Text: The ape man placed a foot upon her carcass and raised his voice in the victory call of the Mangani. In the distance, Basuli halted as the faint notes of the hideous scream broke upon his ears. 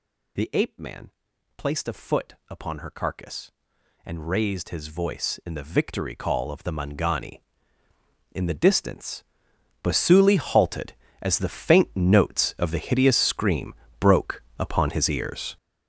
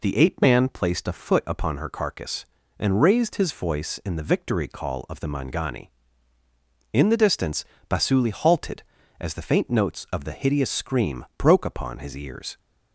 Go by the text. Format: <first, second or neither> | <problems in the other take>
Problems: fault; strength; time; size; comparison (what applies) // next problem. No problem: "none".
second | gets louder; strong; throughout; 11 dB // pauses between "man" and "placed"; noticeable; at 1.0 s; 0.48 s long // pauses between "foot" and "upon"; slight; at 2.3 s; 0.16 s long // pauses between "scream" and "broke"; slight; at 13.7 s; 0.26 s long // pauses between "broke" and "upon"; slight; at 14.4 s; 0.16 s long